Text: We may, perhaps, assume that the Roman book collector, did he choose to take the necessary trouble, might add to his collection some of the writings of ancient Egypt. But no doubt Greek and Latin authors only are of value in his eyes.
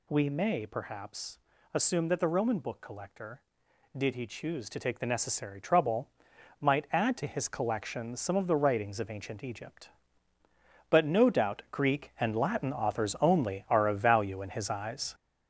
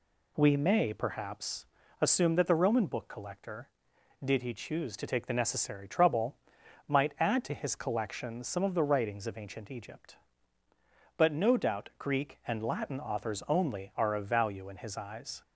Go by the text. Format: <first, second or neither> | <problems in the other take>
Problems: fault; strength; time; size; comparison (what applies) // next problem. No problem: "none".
second | gets louder; throughout; 6.5 dB